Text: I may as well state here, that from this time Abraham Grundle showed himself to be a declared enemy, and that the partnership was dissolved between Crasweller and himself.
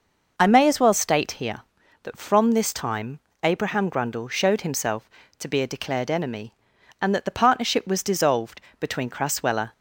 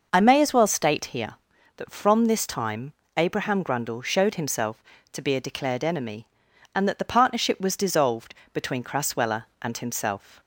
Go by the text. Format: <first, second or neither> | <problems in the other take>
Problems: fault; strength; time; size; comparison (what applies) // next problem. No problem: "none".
second | pauses between "time" and "Abraham"; slight; at 3.2 s; 0.22 s long; slight in the second // pauses between "dissolved" and "between"; slight; at 8.6 s; 0.20 s long; slight in the second // stops before "and himself"; at 9.7 s